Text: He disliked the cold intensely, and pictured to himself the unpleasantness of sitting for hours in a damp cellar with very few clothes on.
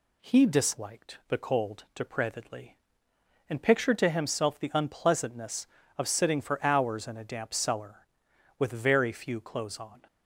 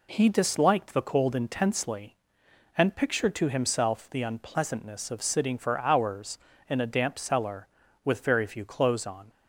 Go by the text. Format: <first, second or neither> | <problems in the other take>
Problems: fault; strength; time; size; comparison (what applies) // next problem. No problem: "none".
second | says "depravedly" for "intensely"; at 1.9 s